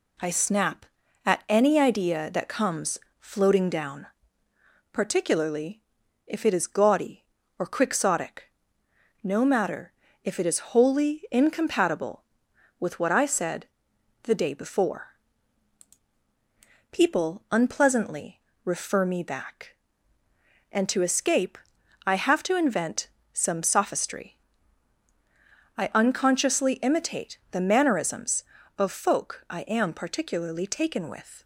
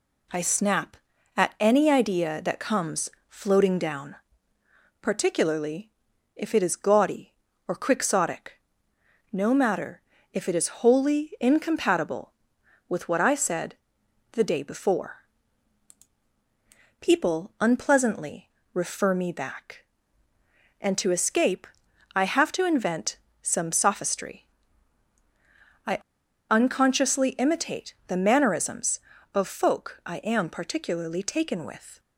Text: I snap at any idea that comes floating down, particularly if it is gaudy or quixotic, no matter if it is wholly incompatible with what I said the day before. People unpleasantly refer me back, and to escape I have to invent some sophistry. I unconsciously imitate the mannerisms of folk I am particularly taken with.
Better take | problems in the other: first | pauses between "comes" and "floating"; slight; at 3.0 s; 0.20 s long; slight in the first // pauses between "particularly" and "if"; noticeable; at 5.8 s; 0.48 s long; noticeable in the first // pauses between "matter" and "if"; slight; at 10.0 s; 0.32 s long; slight in the first // pauses between "said" and "the"; noticeable; at 13.7 s; 0.58 s long; noticeable in the first // pauses between "unpleasantly" and "refer"; slight; at 18.4 s; 0.26 s long; slight in the first // pauses between "escape" and "I"; noticeable; at 21.6 s; 0.48 s long; noticeable in the first // pauses between "invent" and "some"; slight; at 23.1 s; 0.24 s long; slight in the first // pauses between "I" and "unconsciously"; noticeable; at 25.9 s; 0.51 s long

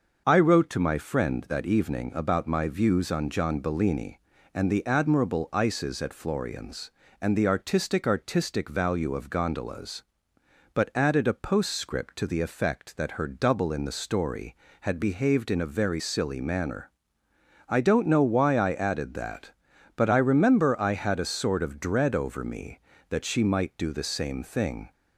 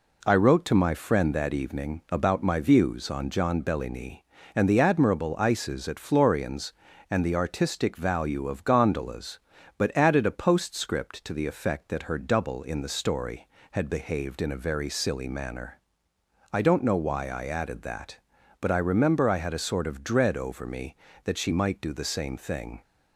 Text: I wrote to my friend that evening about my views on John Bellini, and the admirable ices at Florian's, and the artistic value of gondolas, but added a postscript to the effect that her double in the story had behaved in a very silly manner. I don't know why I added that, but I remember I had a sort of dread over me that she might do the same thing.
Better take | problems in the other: second | starts louder than the rest; noticeable; until 1.2 s; 6 dB // says "artistic" twice; at 8.0 s

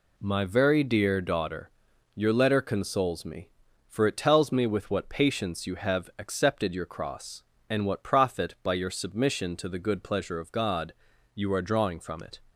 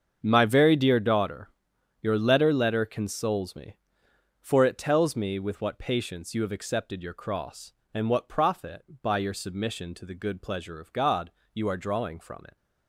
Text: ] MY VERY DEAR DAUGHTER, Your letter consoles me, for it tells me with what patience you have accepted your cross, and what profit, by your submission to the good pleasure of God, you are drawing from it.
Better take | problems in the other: first | starts louder than the rest; until 1.2 s; 7 dB // says "letter" twice; at 2.5 s

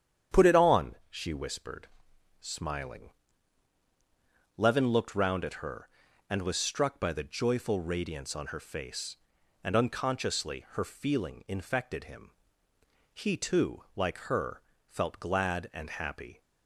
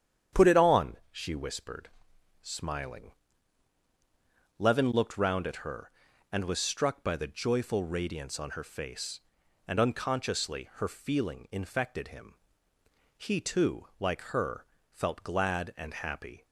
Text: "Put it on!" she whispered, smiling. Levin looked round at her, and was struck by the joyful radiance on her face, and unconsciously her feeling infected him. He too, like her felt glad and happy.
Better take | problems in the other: neither | starts louder than the rest; strong; the same in both // pauses between "her" and "felt"; slight; the same in both

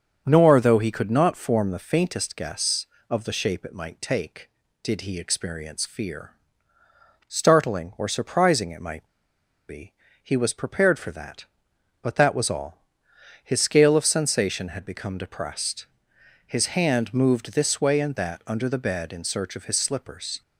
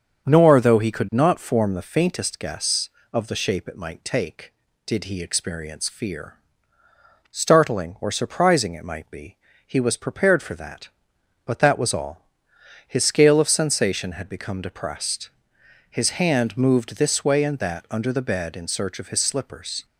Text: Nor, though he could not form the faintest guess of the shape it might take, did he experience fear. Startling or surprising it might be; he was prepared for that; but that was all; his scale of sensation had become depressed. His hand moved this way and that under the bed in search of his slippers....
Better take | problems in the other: second | starts louder than the rest; until 1.2 s; 7 dB; also in the second // pauses between "might" and "be"; noticeable; at 9.0 s; 0.60 s long

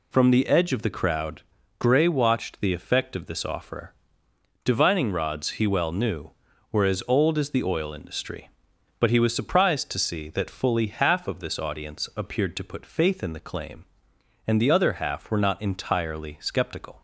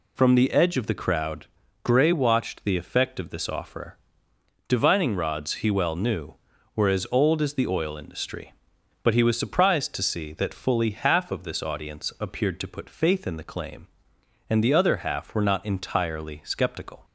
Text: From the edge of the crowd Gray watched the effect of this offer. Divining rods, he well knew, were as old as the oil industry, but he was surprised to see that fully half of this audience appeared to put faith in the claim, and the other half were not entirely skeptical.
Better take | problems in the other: neither | pauses between "crowd" and "Gray"; the same in both

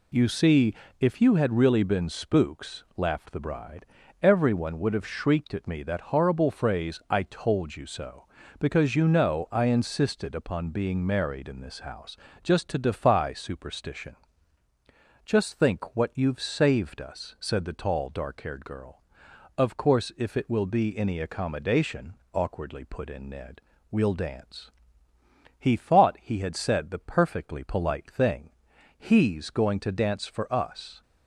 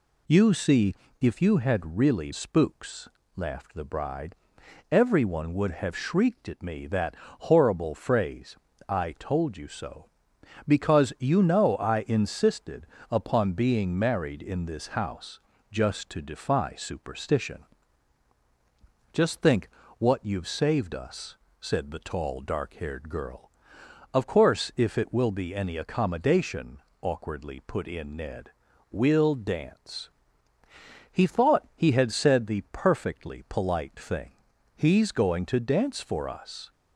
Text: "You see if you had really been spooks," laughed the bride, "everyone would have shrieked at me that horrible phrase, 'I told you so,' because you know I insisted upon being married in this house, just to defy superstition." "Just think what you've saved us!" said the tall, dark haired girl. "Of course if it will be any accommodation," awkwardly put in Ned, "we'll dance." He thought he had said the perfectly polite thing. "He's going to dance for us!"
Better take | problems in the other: first | pauses between "see" and "if"; slight; at 0.9 s; 0.26 s long; slight in the first // skips "been"; at 2.3 s // pauses between "that" and "horrible"; slight; at 7.1 s; 0.24 s long // pauses between "insisted" and "upon"; slight; at 12.8 s; 0.24 s long // pauses between "think" and "what"; slight; at 19.6 s; 0.30 s long

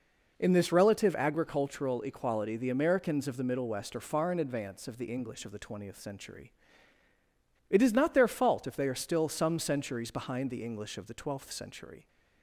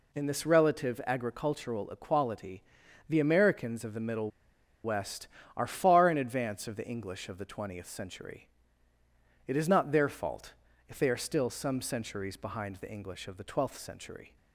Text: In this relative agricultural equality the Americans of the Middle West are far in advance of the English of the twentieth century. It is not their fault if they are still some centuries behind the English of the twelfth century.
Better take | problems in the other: first | pauses between "equality" and "the"; noticeable; at 2.6 s; 0.46 s long // pauses between "Middle" and "West"; noticeable; at 4.2 s; 0.54 s long // pauses between "fault" and "if"; slight; at 10.5 s; 0.34 s long

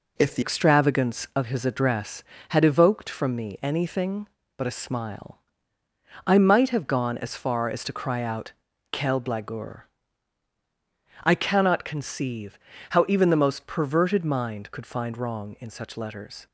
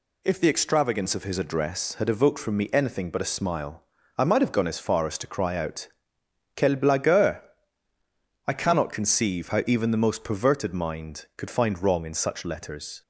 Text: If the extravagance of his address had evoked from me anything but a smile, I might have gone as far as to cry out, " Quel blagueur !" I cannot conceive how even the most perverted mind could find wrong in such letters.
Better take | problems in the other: second | changes voice at "extravagance"; from 0.4 s on; 16.0 s long // pauses between "conceive" and "how"; slight; at 12.5 s; 0.30 s long

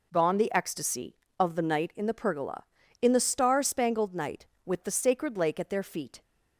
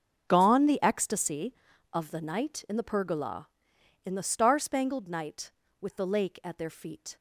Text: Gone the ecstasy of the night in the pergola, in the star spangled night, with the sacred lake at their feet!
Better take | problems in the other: first | starts louder than the rest; until 1.2 s; 6.5 dB // skips "sacred"; at 6.0 s

